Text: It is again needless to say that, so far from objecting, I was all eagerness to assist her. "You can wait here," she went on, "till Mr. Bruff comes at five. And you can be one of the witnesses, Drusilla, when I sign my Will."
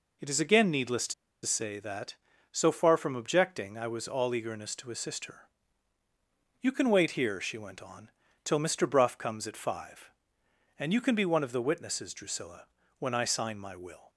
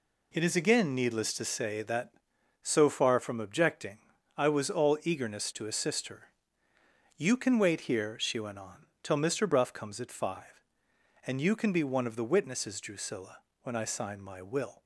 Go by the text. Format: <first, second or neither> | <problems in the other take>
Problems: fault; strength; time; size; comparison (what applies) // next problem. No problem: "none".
second | pauses between "to" and "say"; slight; at 1.1 s; 0.31 s long